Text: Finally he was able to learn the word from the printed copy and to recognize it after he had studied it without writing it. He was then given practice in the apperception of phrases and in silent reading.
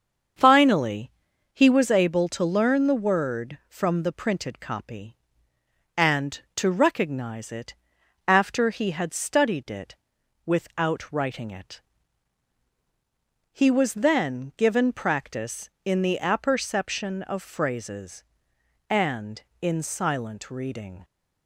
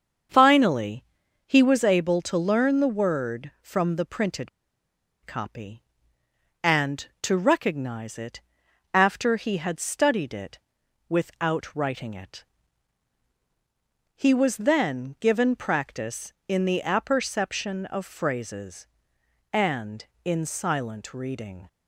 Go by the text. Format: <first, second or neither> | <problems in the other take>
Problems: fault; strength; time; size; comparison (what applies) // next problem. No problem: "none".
first | starts louder than the rest; until 1.7 s; 7 dB; also in the first // pauses between "Finally" and "he"; at 1.0 s; 0.42 s long; also in the first // pauses between "printed" and "copy"; noticeable; at 4.4 s; 0.76 s long // pauses between "it" and "after"; noticeable; at 8.3 s; 0.54 s long; noticeable in the first // pauses between "it" and "without"; noticeable; at 10.5 s; 0.52 s long; noticeable in the first